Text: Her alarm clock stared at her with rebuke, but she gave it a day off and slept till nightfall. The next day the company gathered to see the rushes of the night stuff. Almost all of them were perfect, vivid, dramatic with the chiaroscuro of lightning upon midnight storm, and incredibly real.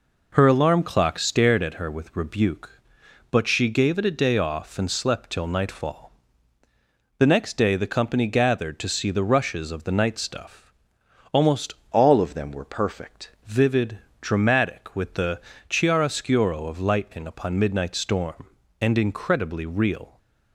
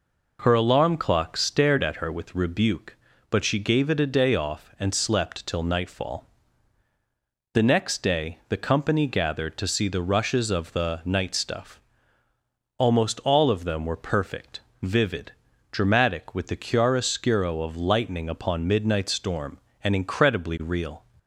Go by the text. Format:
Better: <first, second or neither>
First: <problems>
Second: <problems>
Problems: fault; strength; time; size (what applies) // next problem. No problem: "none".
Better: second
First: changes voice from "all" to "perfect"; from 11.9 to 13.2 s; 1.3 s long // pauses between "the" and "chiaroscuro"; slight; at 15.3 s; 0.30 s long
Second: none